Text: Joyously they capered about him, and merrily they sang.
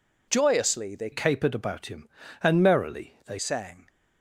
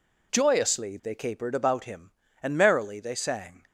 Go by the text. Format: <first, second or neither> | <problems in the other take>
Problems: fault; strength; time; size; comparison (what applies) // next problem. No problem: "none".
second | changes voice from "capered" to "they"; from 1.1 to 3.3 s; 2.2 s long